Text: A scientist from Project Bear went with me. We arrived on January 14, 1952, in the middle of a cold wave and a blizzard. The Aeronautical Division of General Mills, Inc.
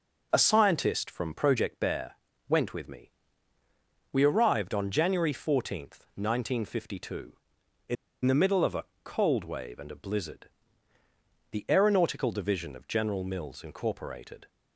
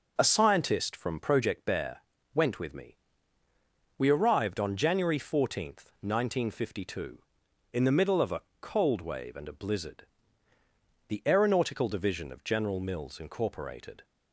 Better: second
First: pauses between "Bear" and "went"; slight; at 2.1 s; 0.36 s long // pauses between "in" and "the"; slight; at 7.9 s; 0.30 s long // pauses between "a" and "cold"; slight; at 8.8 s; 0.18 s long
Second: pauses between "Bear" and "went"; slight; at 1.9 s; 0.36 s long // pauses between "a" and "cold"; slight; at 8.4 s; 0.18 s long

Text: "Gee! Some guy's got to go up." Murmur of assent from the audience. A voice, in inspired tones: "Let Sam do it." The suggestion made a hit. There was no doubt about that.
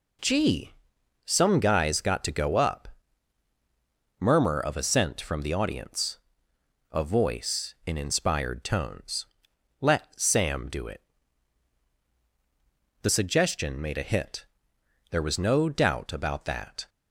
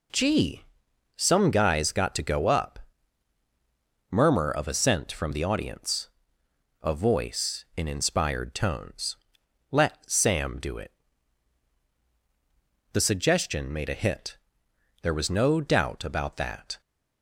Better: neither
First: none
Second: none

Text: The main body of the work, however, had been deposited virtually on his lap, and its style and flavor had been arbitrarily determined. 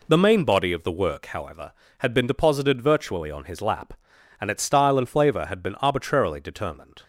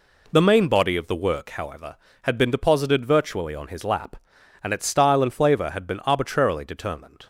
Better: neither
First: none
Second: none

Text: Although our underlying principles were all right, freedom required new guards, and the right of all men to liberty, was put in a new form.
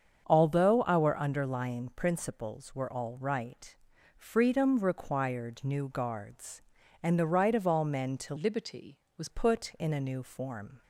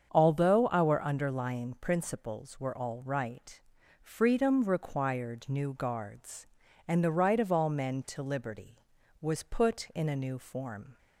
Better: second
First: starts louder than the rest; strong; until 1.2 s; 7 dB // changes voice from "liberty" to "was"; from 8.3 to 9.2 s; 0.9 s long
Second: starts louder than the rest; strong; until 1.1 s; 7 dB

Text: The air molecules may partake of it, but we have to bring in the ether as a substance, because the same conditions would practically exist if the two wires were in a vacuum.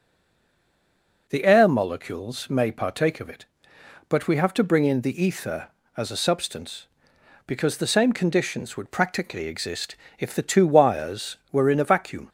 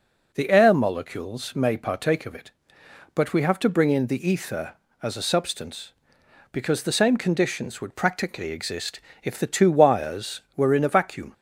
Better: second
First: stays silent before the first word; noticeable; until 1.2 s; 1.2 s long // pauses between "exist" and "if"; slight; at 9.9 s; 0.24 s long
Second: pauses between "exist" and "if"; slight; at 8.9 s; 0.24 s long

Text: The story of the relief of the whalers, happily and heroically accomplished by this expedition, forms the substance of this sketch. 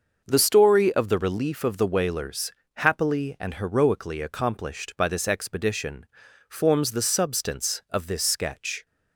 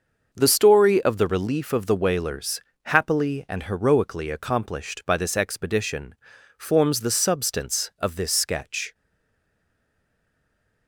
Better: first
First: starts louder than the rest; until 1.2 s; 6 dB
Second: starts louder than the rest; until 1.3 s; 6 dB // stays silent after the last word; noticeable; from 8.9 s on; 1.9 s long

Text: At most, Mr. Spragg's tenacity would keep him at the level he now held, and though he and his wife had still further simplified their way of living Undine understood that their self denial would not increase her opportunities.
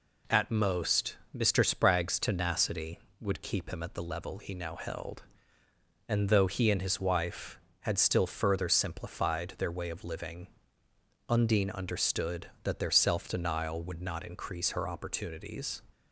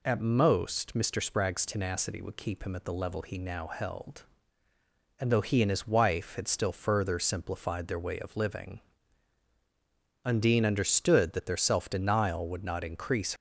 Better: first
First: pauses between "living" and "Undine"; noticeable; at 10.4 s; 0.80 s long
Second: pauses between "living" and "Undine"; strong; at 8.8 s; 1.4 s long // stops before "her opportunities"; at 13.3 s

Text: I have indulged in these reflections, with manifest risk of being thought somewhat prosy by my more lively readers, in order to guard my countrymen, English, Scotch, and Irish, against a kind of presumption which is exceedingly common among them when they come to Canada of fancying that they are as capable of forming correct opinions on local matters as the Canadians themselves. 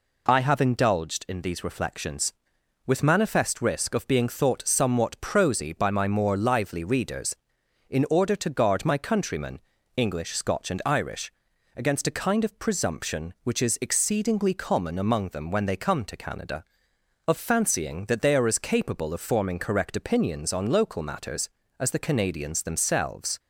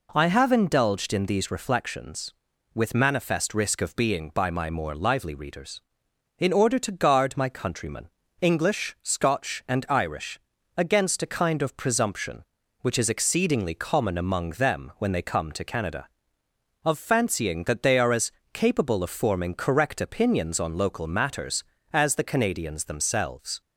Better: first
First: none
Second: skips "thought somewhat prosy"; at 4.3 s // pauses between "as" and "capable"; slight; at 18.3 s; 0.22 s long

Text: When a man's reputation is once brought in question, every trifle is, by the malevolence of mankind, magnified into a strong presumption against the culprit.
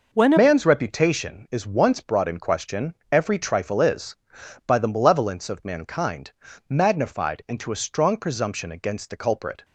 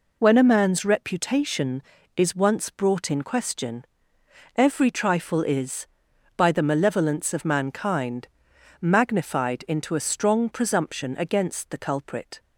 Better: second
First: changes voice at "man's"; from 0.3 s on; 9.3 s long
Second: none

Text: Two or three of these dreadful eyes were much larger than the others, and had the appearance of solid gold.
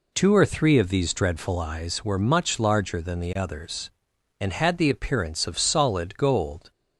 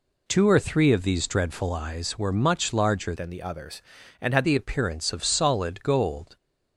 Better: first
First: none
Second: changes voice from "than" to "had"; from 3.1 to 4.4 s; 1.3 s long

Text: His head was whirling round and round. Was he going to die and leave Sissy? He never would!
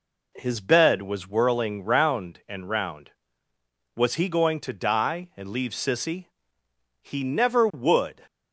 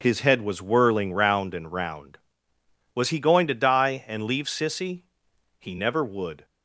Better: second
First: says "bed" for "head"; at 0.5 s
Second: none

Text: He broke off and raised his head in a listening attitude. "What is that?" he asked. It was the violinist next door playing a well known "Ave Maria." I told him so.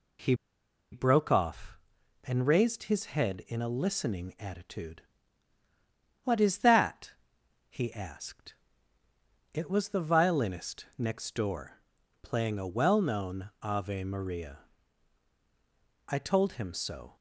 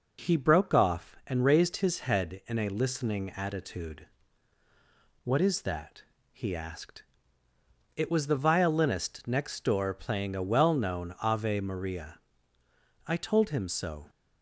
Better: second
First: pauses between "He" and "broke"; noticeable; at 0.3 s; 0.57 s long // pauses between "door" and "playing"; at 11.7 s; 0.42 s long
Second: none

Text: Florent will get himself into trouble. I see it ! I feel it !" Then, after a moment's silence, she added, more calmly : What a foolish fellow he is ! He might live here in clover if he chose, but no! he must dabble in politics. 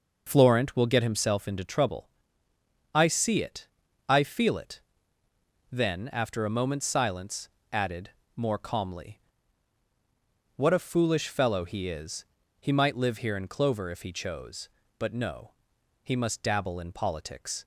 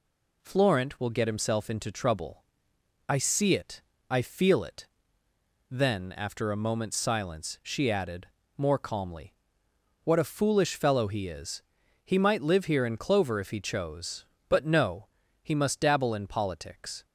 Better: second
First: skips "she"; at 7.5 s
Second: none

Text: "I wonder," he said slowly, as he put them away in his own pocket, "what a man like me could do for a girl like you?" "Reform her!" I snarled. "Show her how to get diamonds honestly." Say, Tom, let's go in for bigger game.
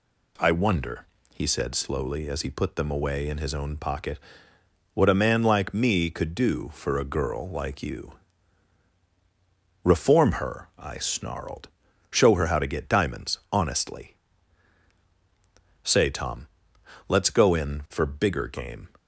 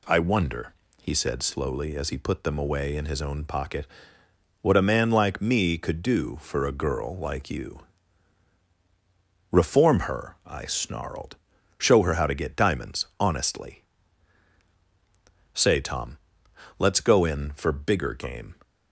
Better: neither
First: none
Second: none

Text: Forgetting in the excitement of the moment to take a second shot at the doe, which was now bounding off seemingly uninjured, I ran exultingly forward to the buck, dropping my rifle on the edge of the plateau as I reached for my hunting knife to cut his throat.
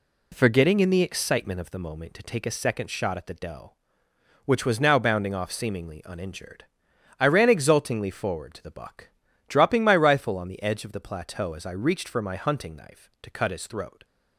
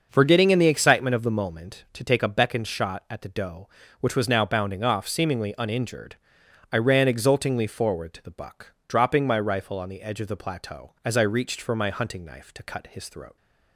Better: first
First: none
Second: starts louder than the rest; until 1.1 s; 6.5 dB // says "beckoned" for "second"; at 2.2 s

